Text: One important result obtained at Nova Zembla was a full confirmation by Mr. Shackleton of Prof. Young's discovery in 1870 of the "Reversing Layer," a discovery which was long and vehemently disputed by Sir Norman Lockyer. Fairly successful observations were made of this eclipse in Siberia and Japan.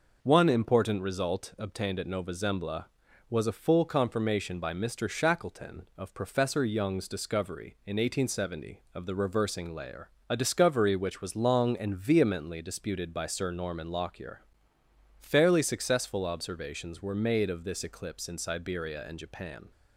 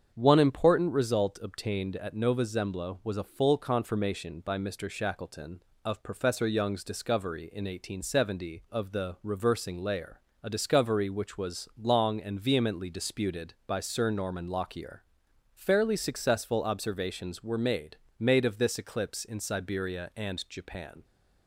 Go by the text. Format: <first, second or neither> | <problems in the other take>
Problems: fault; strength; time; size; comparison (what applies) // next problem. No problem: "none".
first | starts louder than the rest; strong; until 1.1 s; 7.5 dB // says "made" twice; at 18.1 s